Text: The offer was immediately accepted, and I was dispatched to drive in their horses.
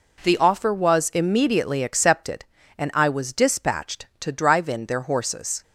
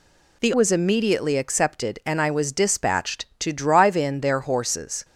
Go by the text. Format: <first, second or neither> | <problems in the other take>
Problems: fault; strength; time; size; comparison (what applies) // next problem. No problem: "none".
first | skips "offer"; at 0.5 s